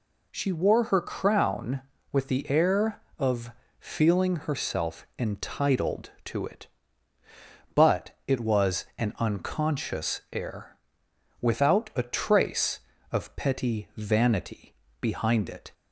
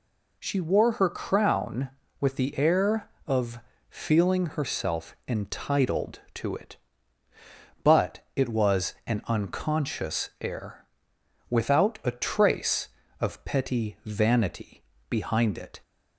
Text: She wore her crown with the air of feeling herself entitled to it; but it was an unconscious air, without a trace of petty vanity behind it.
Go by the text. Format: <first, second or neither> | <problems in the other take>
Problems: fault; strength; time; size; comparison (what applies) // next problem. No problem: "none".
neither | pauses between "of" and "feeling"; slight; the same in both // pauses between "but" and "it"; slight; the same in both // pauses between "vanity" and "behind"; slight; the same in both